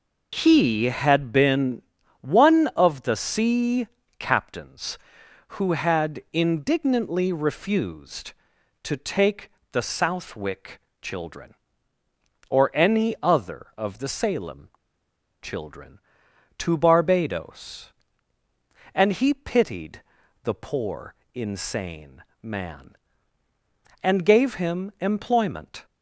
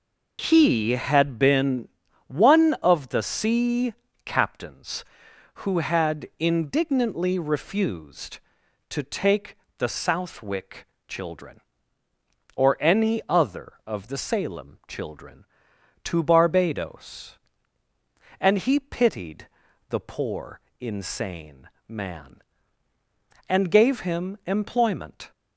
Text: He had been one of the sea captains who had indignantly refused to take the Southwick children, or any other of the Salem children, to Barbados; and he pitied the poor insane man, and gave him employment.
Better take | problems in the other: second | pauses between "been" and "one"; at 1.8 s; 0.40 s long; also in the second // pauses between "sea" and "captains"; slight; at 3.8 s; 0.32 s long; slight in the second // pauses between "take" and "the"; slight; at 9.5 s; 0.18 s long; slight in the second // pauses between "Southwick" and "children"; slight; at 10.7 s; 0.22 s long; slight in the second // pauses between "Salem" and "children"; noticeable; at 14.6 s; 0.73 s long // pauses between "pitied" and "the"; at 20.0 s; 0.44 s long; also in the second // pauses between "poor" and "insane"; slight; at 21.1 s; 0.22 s long; slight in the second // pauses between "insane" and "man"; slight; at 22.2 s; 0.18 s long; slight in the second

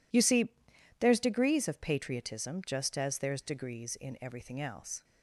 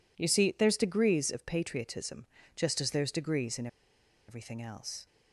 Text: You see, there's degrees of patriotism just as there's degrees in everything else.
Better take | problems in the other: first | pauses between "patriotism" and "just"; slight; at 2.2 s; 0.30 s long // pauses between "in" and "everything"; noticeable; at 3.6 s; 0.61 s long

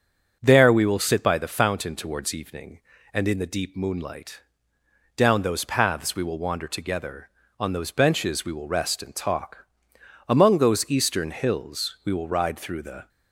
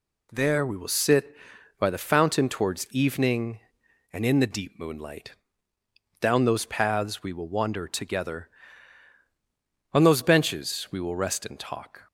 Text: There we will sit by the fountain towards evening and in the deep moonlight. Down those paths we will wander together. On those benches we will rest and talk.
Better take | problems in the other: second | starts louder than the rest; until 1.4 s; 6.5 dB // goes on to say "Among those eastern hills we will ride through the"; strong; from 10.2 s on; 2.8 s long

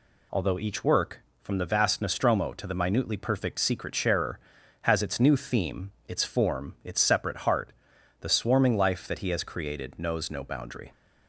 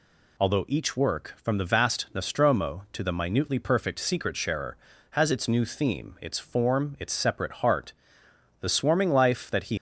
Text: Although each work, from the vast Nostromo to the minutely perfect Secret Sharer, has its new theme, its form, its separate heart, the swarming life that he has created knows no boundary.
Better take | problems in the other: first | stops before "has created knows no boundary"; at 9.7 s

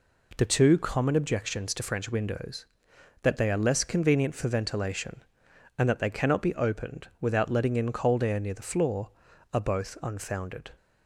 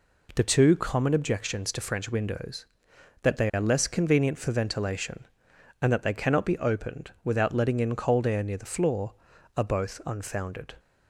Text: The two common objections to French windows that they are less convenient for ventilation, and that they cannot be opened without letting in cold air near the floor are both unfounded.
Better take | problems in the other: neither | none

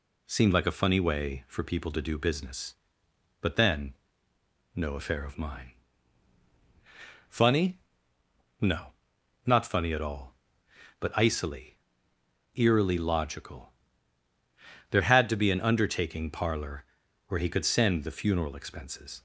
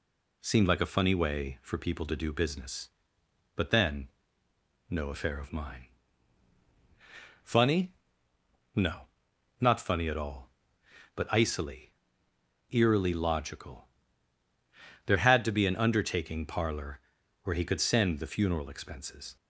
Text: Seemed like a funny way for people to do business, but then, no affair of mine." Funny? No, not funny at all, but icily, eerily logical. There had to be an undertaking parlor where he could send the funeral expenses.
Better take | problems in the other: neither | pauses between "parlor" and "where"; the same in both

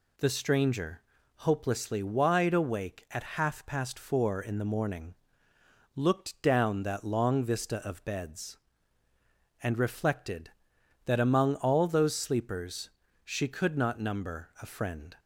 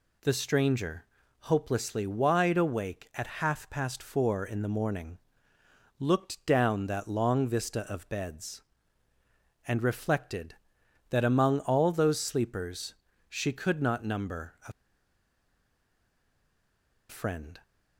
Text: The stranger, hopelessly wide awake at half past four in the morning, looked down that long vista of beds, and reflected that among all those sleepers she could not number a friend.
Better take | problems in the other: first | pauses between "sleepers" and "she"; slight; at 12.9 s; 0.34 s long; slight in the first // pauses between "a" and "friend"; strong; at 14.7 s; 2.3 s long

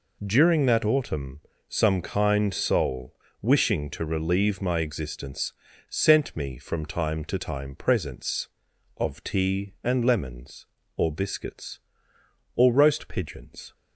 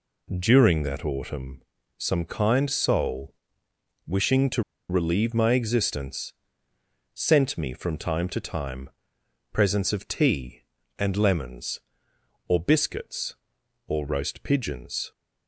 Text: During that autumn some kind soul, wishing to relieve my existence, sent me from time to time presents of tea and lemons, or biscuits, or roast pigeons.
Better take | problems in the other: first | pauses between "autumn" and "some"; slight; at 1.6 s; 0.34 s long; slight in the first // pauses between "to" and "relieve"; slight; at 4.6 s; 0.28 s long // pauses between "time" and "presents"; noticeable; at 8.8 s; 0.62 s long

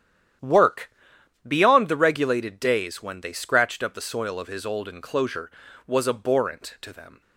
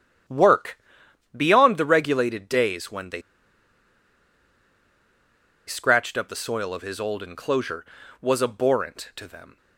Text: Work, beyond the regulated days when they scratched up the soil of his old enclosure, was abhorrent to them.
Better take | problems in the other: first | starts louder than the rest; strong; until 1.8 s; 10 dB; strong in the first // pauses between "they" and "scratched"; strong; at 3.2 s; 2.4 s long

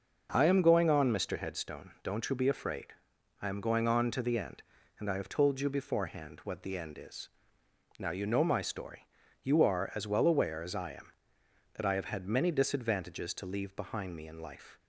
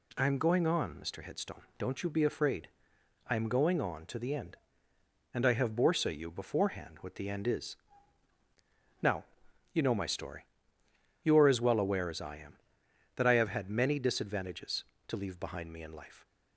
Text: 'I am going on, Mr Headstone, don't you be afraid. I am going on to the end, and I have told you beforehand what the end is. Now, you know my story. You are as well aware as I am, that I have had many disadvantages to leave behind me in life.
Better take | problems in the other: first | says "borsa" for "told"; at 5.7 s

